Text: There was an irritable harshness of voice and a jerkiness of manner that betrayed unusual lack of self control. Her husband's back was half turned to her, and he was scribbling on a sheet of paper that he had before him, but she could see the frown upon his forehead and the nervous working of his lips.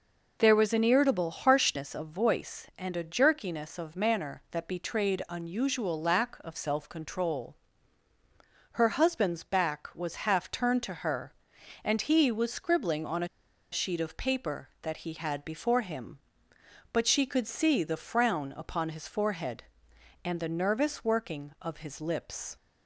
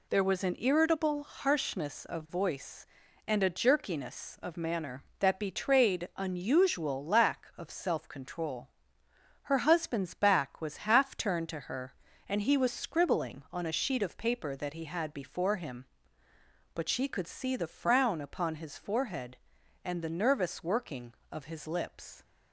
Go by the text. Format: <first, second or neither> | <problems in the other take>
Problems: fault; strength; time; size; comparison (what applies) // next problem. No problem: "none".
second | pauses between "a" and "sheet"; at 13.2 s; 0.44 s long